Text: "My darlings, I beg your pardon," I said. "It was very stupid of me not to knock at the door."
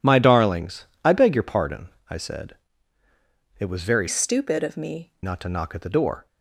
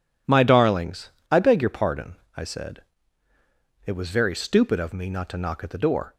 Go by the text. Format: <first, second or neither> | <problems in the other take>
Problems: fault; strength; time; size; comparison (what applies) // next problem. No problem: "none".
second | changes voice from "stupid" to "me"; from 4.0 to 5.1 s; 1.1 s long